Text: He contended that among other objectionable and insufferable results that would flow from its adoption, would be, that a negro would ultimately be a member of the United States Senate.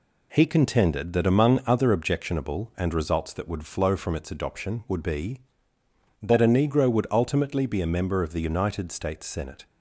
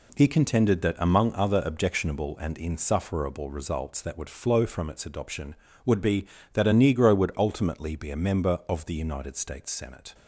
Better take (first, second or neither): second